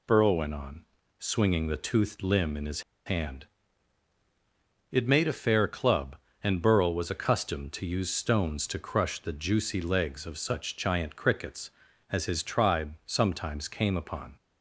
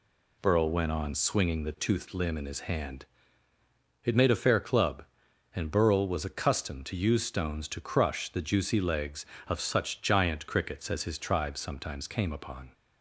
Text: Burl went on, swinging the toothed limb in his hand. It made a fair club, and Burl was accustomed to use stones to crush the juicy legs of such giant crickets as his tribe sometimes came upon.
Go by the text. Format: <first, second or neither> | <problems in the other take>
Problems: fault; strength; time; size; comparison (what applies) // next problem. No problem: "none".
second | pauses between "his" and "hand"; slight; at 2.8 s; 0.24 s long